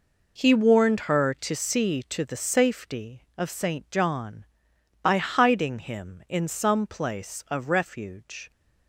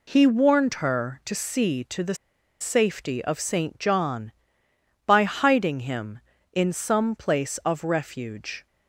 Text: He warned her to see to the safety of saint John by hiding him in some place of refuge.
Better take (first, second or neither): first